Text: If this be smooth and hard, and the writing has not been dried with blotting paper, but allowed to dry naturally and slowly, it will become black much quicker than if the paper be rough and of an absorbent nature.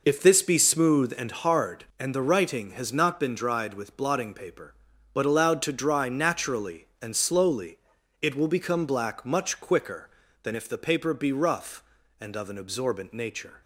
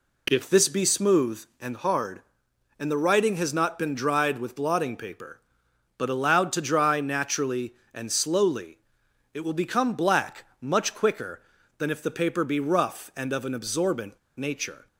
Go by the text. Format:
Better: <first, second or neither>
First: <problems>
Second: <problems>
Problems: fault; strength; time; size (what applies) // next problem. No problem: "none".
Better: first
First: none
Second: pauses between "black" and "much"; slight; at 10.4 s; 0.16 s long // pauses between "absorbent" and "nature"; slight; at 14.1 s; 0.18 s long